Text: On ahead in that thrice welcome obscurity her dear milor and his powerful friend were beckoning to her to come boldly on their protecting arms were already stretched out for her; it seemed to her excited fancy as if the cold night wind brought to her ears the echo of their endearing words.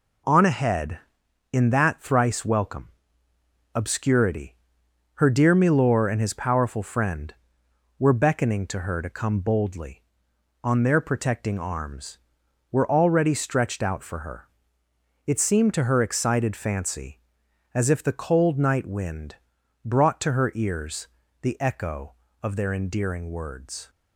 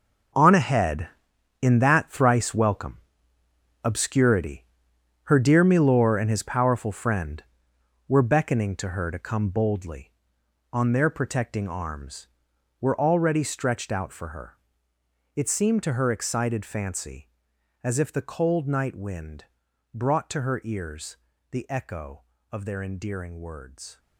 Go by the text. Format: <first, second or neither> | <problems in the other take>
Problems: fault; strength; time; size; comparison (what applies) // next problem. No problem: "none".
first | gets quieter; strong; throughout; 13 dB // pauses between "welcome" and "obscurity"; noticeable; at 2.9 s; 0.88 s long; noticeable in the first // pauses between "obscurity" and "her"; noticeable; at 4.6 s; 0.60 s long; noticeable in the first // pauses between "wind" and "brought"; noticeable; at 19.4 s; 0.48 s long; noticeable in the first // pauses between "ears" and "the"; slight; at 21.1 s; 0.34 s long; slight in the first